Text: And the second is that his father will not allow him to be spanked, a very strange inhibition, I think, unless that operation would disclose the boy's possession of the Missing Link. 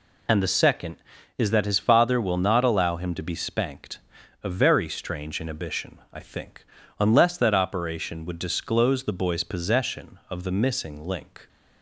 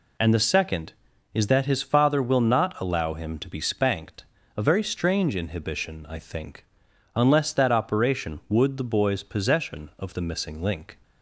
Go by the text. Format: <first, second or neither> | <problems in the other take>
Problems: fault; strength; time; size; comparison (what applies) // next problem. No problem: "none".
first | skips "disclose"; at 8.7 s